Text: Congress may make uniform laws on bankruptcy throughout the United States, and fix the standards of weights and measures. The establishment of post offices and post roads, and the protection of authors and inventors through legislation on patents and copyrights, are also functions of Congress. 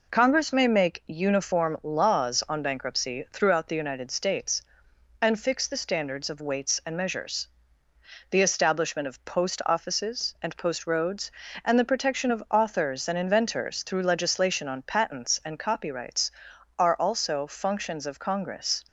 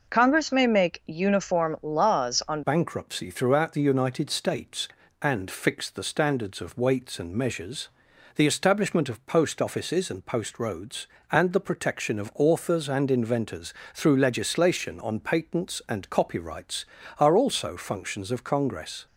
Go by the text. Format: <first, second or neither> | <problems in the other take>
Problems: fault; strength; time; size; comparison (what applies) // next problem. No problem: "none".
first | changes voice at "bankruptcy"; from 2.6 s on; 16.4 s long // pauses between "inventors" and "through"; slight; at 13.7 s; 0.20 s long